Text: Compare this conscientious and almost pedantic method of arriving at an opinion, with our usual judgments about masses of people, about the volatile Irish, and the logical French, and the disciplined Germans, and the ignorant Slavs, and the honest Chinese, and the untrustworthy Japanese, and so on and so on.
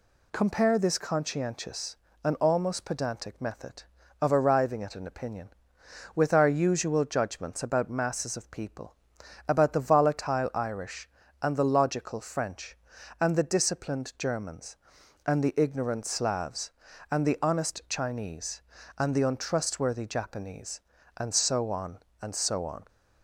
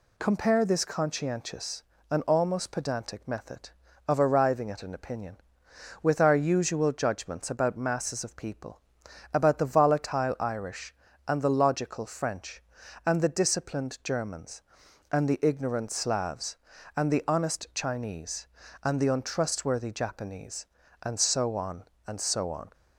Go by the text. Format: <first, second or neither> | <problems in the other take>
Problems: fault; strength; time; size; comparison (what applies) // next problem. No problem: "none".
neither | none